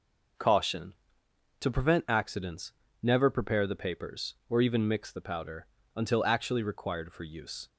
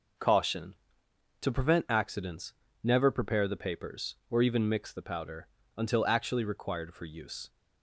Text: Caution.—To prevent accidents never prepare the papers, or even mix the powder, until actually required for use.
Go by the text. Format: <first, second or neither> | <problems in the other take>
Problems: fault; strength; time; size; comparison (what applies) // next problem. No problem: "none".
neither | pauses between "accidents" and "never"; slight; the same in both